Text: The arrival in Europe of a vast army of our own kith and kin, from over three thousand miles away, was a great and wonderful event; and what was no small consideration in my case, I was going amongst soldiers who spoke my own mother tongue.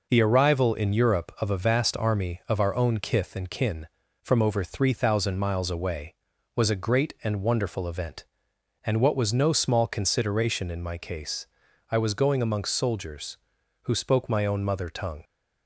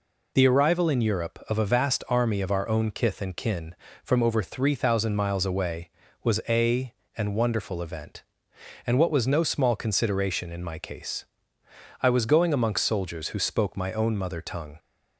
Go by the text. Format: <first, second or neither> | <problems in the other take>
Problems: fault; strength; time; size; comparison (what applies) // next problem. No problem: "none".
first | skips "great"; at 7.0 s